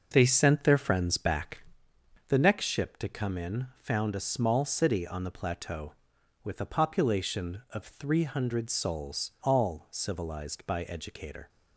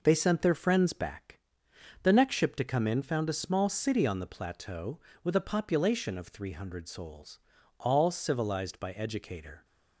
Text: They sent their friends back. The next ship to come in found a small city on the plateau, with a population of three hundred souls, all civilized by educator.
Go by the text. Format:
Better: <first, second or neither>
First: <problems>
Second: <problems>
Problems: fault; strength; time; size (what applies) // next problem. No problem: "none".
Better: neither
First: none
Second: none